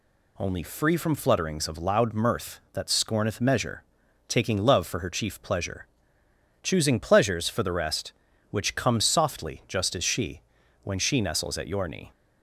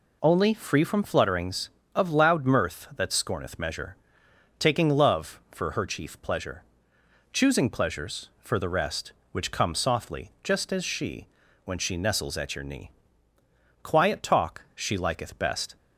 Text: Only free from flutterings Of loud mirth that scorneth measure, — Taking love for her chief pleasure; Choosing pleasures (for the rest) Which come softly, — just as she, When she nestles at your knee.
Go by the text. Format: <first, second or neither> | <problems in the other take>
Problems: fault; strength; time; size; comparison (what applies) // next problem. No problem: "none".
first | goes on to say "Quiet talk she liketh best"; strong; from 13.8 s on; 1.9 s long